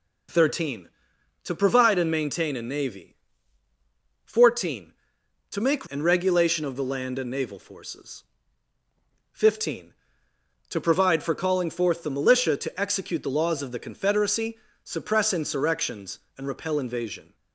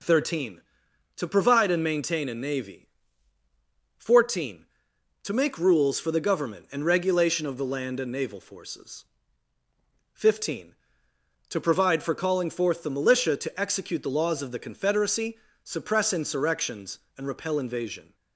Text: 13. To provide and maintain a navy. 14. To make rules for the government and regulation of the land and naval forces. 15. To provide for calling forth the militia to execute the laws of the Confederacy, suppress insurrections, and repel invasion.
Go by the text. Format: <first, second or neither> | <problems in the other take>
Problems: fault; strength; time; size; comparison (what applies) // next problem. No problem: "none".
second | skips "rules for the government"; at 5.8 s